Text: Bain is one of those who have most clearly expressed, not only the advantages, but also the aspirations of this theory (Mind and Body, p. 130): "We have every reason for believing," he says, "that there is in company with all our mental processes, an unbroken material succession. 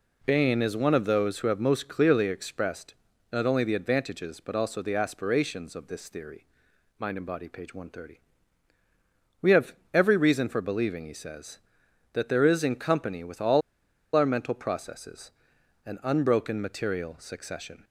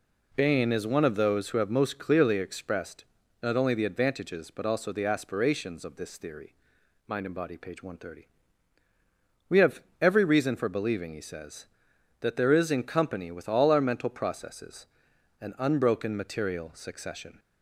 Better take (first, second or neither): second